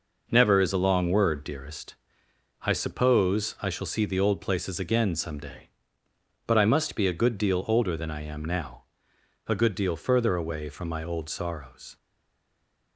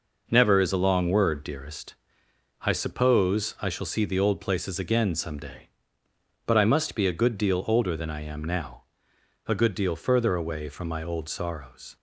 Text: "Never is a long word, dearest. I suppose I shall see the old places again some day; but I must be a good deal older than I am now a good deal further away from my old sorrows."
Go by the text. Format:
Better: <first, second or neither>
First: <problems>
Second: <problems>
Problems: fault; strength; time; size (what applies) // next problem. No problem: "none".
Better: second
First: pauses between "now" and "a"; noticeable; at 8.8 s; 0.66 s long // stays silent after the last word; from 11.9 s on; 1.0 s long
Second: pauses between "now" and "a"; noticeable; at 8.8 s; 0.66 s long